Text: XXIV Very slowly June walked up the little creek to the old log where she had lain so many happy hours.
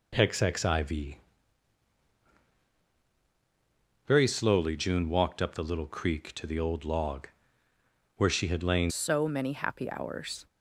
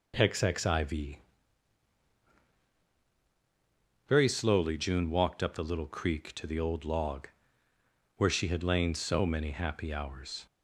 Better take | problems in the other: second | pauses between "XXIV" and "Very"; strong; at 1.1 s; 2.9 s long; strong in the second // pauses between "log" and "where"; noticeable; at 7.2 s; 0.90 s long; noticeable in the second // changes voice at "so"; from 8.8 s on; 1.6 s long

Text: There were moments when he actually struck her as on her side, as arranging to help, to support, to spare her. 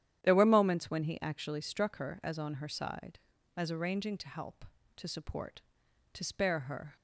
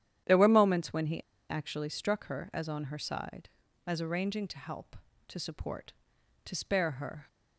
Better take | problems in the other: first | starts louder than the rest; strong; until 1.5 s; 10.5 dB; strong in the first // pauses between "he" and "actually"; slight; at 1.1 s; 0.29 s long

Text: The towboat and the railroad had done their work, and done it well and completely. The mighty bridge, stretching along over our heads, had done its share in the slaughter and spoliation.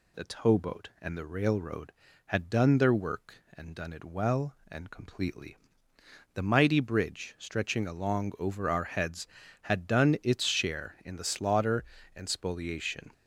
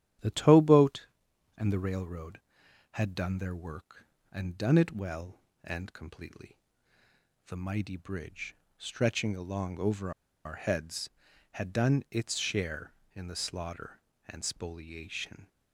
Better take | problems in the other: first | starts louder than the rest; strong; until 1.7 s; 11.5 dB // pauses between "over" and "our"; slight; at 10.1 s; 0.34 s long

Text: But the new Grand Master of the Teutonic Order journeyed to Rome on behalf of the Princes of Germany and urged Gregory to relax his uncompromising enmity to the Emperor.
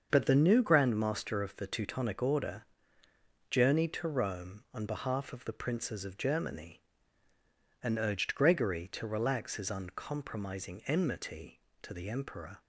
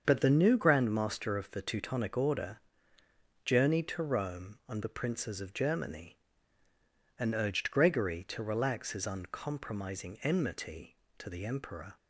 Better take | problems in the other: first | starts louder than the rest; until 1.0 s; 7 dB; also in the first // pauses between "Order" and "journeyed"; noticeable; at 2.5 s; 0.84 s long; noticeable in the first // skips "behalf of"; at 4.8 s

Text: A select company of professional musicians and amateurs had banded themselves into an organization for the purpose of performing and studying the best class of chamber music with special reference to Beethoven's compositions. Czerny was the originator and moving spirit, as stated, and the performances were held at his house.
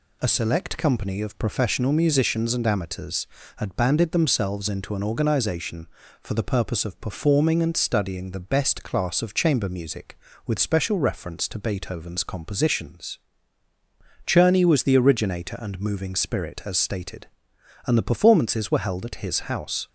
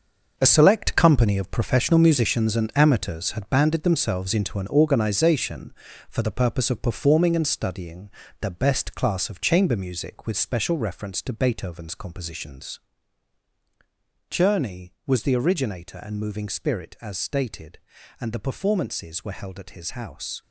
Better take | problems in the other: first | gets quieter; strong; throughout; 10.5 dB // pauses between "studying" and "the"; slight; at 8.1 s; 0.30 s long

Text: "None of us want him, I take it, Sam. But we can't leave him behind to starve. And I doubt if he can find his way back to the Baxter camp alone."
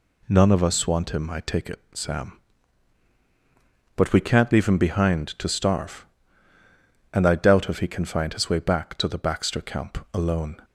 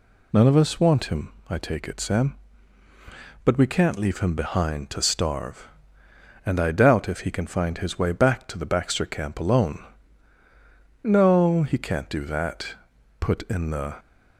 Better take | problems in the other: first | goes on to say "No he can't do that put in the"; strong; from 11.0 s on; 2.9 s long

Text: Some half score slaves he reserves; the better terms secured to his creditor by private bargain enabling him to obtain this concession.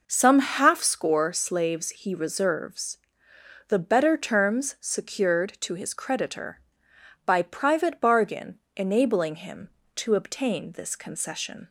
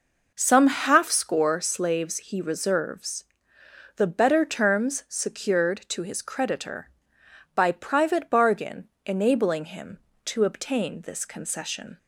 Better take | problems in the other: neither | pauses between "bargain" and "enabling"; slight; the same in both

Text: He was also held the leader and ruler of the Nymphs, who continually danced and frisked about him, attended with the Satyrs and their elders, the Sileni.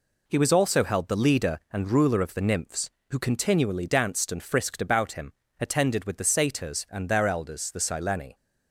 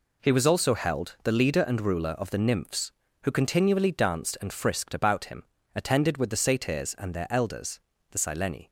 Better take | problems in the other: neither | none

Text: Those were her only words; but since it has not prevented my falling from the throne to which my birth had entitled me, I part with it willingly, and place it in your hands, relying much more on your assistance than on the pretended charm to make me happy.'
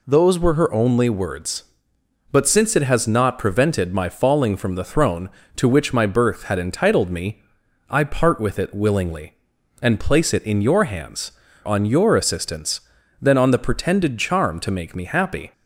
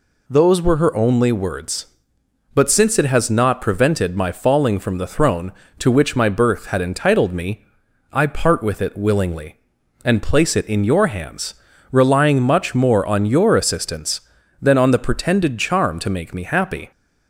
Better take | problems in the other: second | skips "relying much more"; at 11.4 s

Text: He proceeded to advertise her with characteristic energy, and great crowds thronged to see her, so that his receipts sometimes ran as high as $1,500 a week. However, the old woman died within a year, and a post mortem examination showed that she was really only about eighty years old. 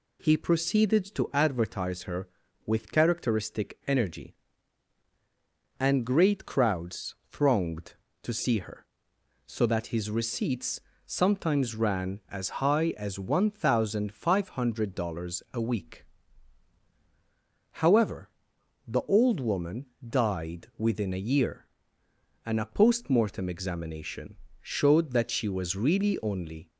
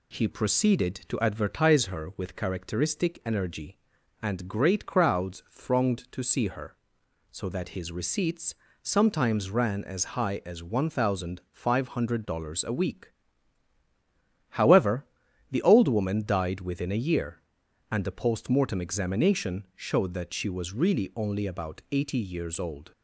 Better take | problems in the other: second | pauses between "crowds" and "thronged"; slight; at 7.1 s; 0.16 s long // pauses between "receipts" and "sometimes"; slight; at 10.7 s; 0.28 s long; slight in the second // pauses between "woman" and "died"; slight; at 19.8 s; 0.20 s long // pauses between "examination" and "showed"; slight; at 24.3 s; 0.24 s long // stops before "about eighty years old"; at 26.6 s

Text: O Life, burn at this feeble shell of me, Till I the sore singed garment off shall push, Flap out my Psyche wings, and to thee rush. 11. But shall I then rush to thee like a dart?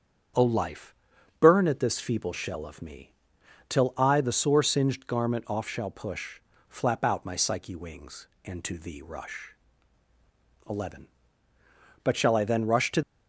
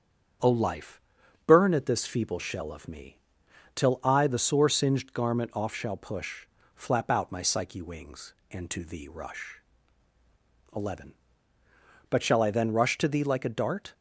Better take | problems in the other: second | starts louder than the rest; strong; until 1.8 s; 8 dB; strong in the second // stops before "thee like a dart"; at 13.0 s

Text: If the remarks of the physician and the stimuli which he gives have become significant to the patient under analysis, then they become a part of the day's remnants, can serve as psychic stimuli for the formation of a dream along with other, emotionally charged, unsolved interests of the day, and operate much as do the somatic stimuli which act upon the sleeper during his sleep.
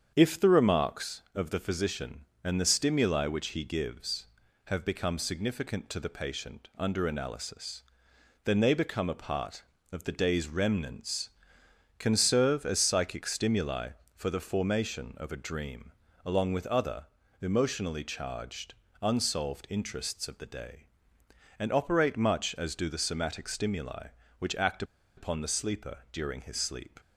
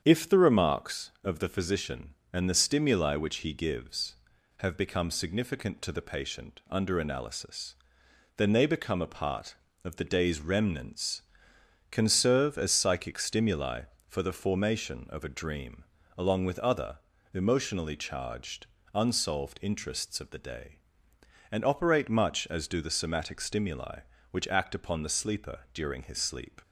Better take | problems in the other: second | starts louder than the rest; strong; until 1.1 s; 8 dB; strong in the second // pauses between "dream" and "along"; slight; at 15.9 s; 0.32 s long; slight in the second // pauses between "act" and "upon"; slight; at 24.8 s; 0.33 s long

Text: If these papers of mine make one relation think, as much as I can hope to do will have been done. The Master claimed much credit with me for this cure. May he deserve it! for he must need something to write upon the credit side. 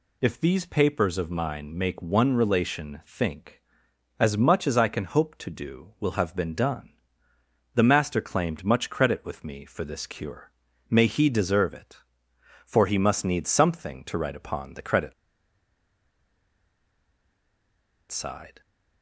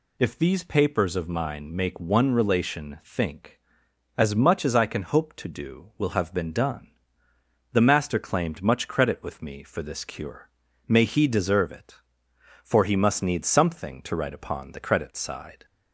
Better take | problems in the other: second | pauses between "credit" and "side"; strong; at 15.1 s; 2.9 s long

